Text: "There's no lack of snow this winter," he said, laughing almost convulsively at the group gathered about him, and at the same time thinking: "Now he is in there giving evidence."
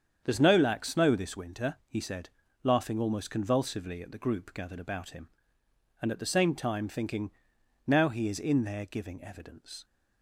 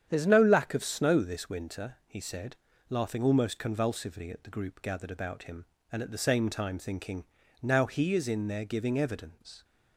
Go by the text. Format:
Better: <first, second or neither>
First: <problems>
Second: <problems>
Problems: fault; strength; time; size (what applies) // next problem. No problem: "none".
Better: second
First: starts louder than the rest; strong; until 1.2 s; 7.5 dB // skips "of"; at 0.8 s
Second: starts louder than the rest; strong; until 1.1 s; 8.5 dB